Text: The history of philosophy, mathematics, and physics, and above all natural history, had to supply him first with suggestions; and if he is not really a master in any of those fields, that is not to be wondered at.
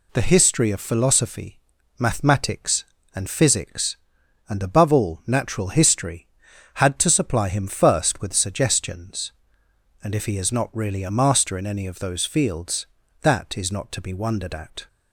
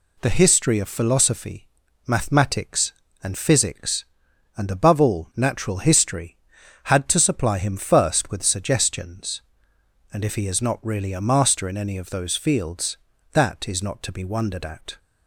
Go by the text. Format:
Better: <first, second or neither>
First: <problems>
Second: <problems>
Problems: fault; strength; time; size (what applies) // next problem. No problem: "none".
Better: neither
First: none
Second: none